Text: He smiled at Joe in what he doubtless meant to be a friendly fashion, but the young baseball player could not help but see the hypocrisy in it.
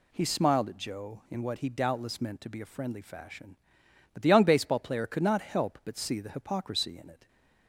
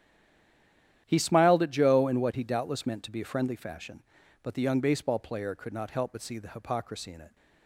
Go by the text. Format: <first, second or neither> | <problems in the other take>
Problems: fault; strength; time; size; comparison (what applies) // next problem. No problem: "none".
first | stays silent before the first word; until 1.0 s; 1.0 s long // starts louder than the rest; strong; until 2.0 s; 10.5 dB